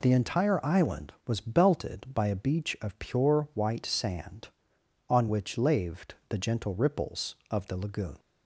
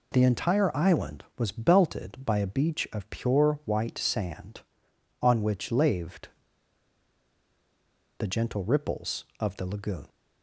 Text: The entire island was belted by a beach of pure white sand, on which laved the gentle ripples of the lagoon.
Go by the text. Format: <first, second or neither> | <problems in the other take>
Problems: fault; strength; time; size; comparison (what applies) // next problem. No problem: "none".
first | pauses between "laved" and "the"; strong; at 6.2 s; 1.8 s long